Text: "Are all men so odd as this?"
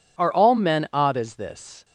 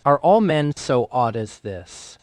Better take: second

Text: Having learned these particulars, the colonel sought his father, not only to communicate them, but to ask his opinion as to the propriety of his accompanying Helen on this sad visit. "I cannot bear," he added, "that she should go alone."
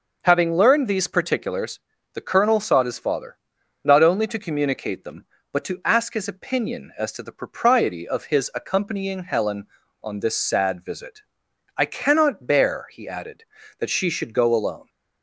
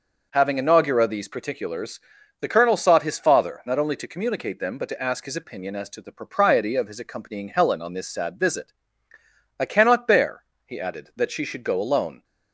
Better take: first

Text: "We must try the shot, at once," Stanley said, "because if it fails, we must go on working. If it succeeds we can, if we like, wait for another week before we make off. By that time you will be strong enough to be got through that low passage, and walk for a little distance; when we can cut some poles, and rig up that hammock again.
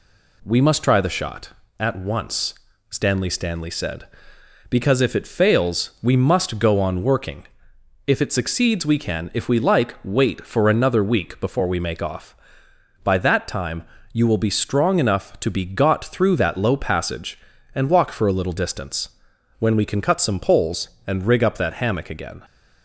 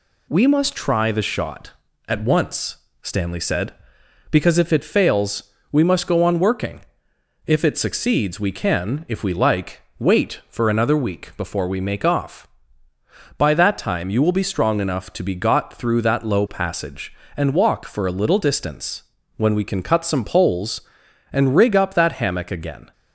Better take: second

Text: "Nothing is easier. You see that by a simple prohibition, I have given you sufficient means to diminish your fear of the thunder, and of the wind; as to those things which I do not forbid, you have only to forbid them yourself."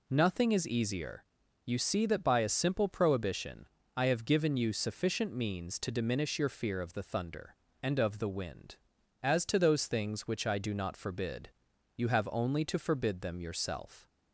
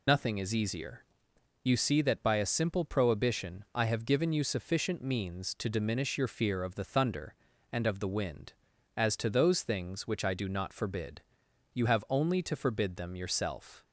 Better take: first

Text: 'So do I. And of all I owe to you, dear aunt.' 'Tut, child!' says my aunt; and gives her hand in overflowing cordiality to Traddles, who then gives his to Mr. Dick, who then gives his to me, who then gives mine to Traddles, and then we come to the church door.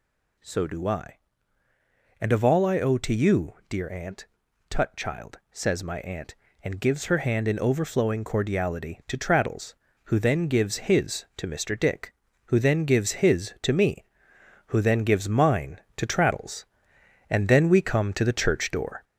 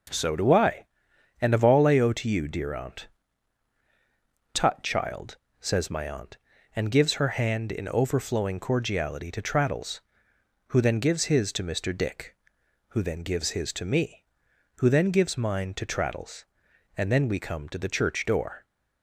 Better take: second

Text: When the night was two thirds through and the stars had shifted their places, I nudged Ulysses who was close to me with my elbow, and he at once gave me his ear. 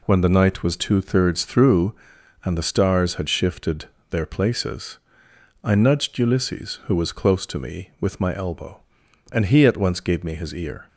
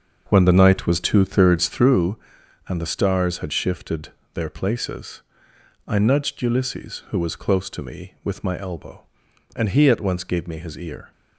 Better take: first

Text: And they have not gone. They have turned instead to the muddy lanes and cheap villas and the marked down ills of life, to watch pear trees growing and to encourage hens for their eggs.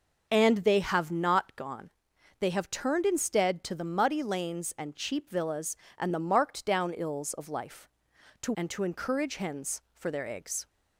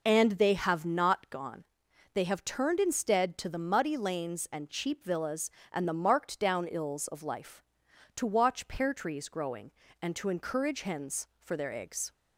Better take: second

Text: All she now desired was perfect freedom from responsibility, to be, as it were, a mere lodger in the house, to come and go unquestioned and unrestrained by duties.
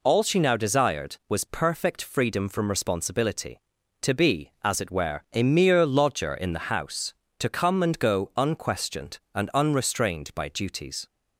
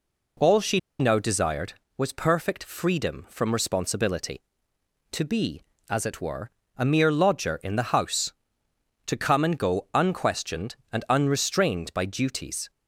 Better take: first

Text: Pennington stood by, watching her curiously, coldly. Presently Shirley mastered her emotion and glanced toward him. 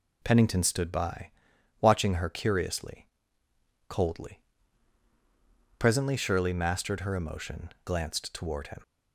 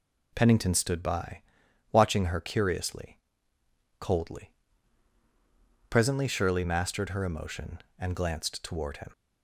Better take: second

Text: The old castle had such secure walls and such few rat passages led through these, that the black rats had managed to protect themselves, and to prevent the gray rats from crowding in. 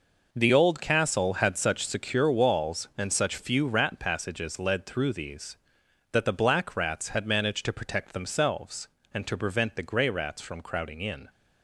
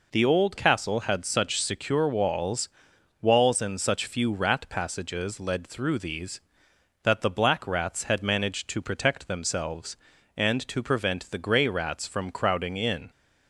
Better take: first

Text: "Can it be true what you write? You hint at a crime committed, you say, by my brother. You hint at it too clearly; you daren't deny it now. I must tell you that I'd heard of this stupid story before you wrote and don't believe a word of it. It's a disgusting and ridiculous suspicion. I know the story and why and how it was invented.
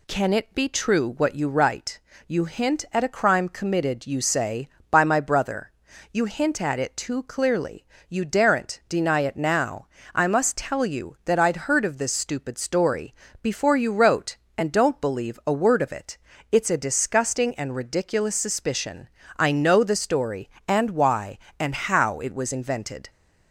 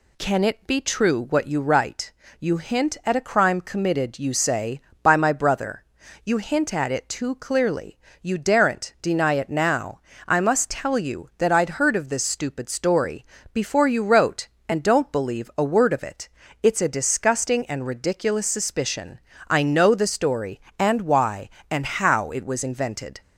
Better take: neither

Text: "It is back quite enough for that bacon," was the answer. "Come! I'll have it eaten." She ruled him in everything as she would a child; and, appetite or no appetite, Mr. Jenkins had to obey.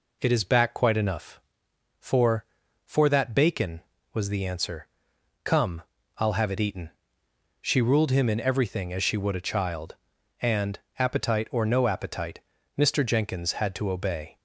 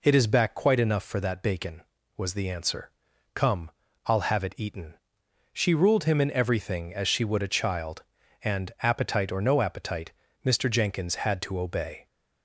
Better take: second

